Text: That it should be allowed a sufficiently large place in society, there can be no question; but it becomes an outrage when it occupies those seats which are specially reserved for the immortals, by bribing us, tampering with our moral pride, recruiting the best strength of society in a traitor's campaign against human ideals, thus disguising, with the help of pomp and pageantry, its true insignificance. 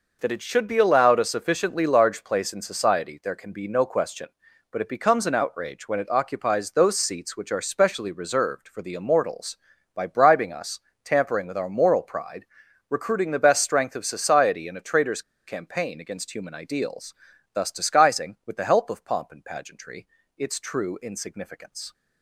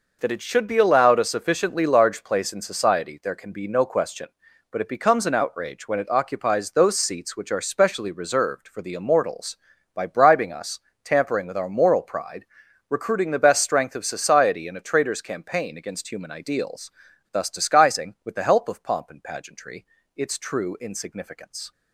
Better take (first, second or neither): second